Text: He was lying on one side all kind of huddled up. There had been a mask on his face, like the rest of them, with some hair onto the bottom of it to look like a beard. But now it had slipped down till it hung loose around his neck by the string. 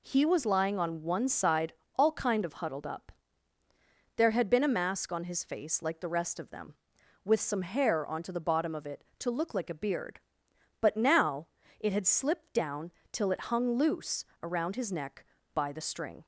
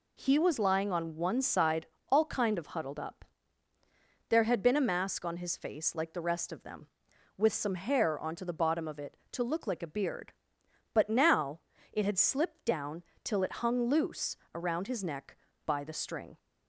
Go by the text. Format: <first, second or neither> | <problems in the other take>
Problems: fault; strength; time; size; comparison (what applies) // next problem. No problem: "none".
neither | pauses between "side" and "all"; slight; the same in both // pauses between "now" and "it"; slight; the same in both // pauses between "down" and "till"; slight; the same in both // pauses between "loose" and "around"; slight; the same in both